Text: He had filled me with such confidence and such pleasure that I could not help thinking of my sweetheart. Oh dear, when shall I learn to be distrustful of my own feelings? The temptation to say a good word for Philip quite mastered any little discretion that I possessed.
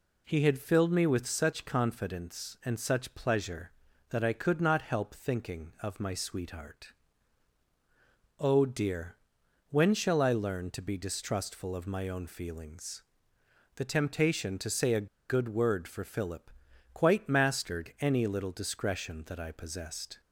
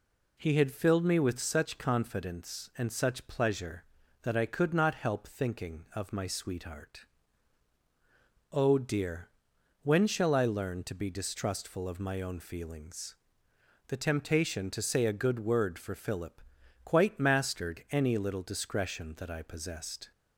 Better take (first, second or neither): second